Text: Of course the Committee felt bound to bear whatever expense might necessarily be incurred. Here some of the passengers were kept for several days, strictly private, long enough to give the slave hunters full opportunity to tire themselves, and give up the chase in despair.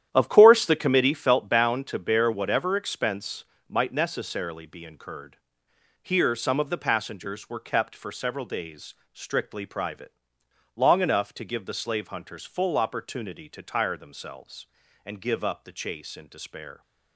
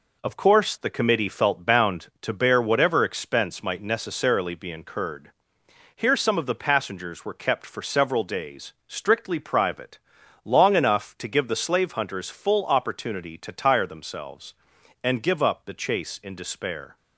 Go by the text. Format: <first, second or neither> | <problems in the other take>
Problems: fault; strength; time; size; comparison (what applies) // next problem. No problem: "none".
second | starts louder than the rest; strong; until 1.2 s; 10.5 dB // pauses between "expense" and "might"; slight; at 3.4 s; 0.24 s long